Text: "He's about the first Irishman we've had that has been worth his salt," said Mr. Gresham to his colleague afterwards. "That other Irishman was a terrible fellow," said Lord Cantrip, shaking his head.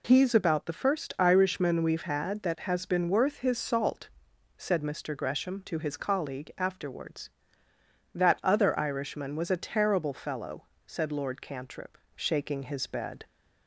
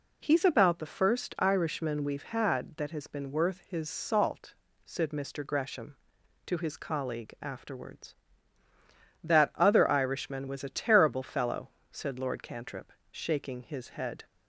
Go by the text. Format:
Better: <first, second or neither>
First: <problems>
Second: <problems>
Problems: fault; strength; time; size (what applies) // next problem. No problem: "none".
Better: second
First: says "bed" for "head"; at 12.8 s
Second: none